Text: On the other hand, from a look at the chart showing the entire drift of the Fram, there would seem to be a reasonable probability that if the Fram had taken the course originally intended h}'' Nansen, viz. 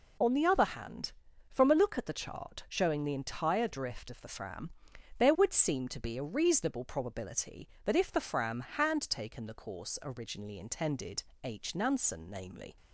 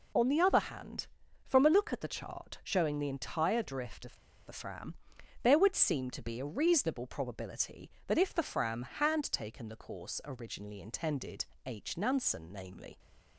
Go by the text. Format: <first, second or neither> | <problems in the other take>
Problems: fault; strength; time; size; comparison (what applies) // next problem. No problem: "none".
first | pauses between "of" and "the"; slight; at 4.1 s; 0.32 s long // pauses between "intended" and "h"; slight; at 11.4 s; 0.22 s long; slight in the first